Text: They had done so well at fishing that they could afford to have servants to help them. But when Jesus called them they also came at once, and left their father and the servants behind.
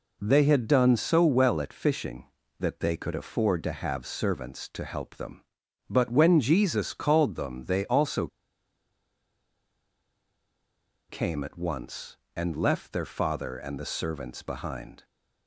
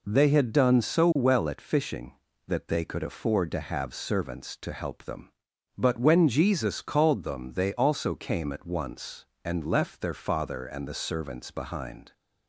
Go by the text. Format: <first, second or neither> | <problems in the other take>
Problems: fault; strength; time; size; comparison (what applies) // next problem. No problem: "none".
second | pauses between "also" and "came"; strong; at 8.2 s; 2.8 s long